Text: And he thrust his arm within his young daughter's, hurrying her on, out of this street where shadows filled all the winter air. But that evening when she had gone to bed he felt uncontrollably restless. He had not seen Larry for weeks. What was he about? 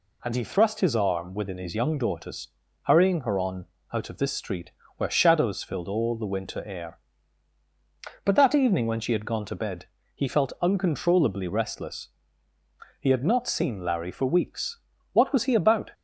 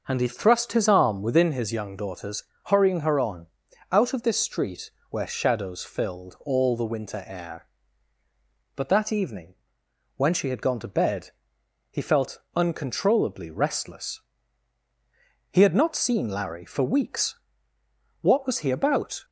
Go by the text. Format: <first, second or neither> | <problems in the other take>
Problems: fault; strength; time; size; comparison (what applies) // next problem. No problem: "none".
first | starts louder than the rest; noticeable; until 1.5 s; 6 dB // pauses between "street" and "where"; slight; at 4.8 s; 0.20 s long; slight in the first // pauses between "evening" and "when"; noticeable; at 9.5 s; 0.60 s long // pauses between "bed" and "he"; noticeable; at 11.3 s; 0.60 s long; slight in the first // pauses between "felt" and "uncontrollably"; slight; at 12.3 s; 0.16 s long